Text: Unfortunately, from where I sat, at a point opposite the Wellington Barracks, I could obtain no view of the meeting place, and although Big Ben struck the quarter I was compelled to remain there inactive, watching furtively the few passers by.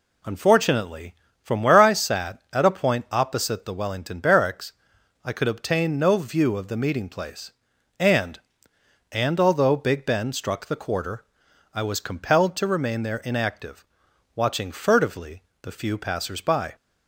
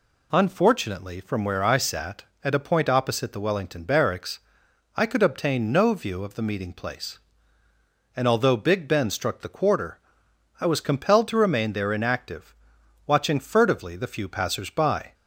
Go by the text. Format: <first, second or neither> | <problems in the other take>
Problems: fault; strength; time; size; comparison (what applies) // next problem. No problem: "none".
second | says "and" twice; at 9.1 s // pauses between "quarter" and "I"; noticeable; at 11.2 s; 0.50 s long; noticeable in the second // pauses between "furtively" and "the"; slight; at 15.4 s; 0.22 s long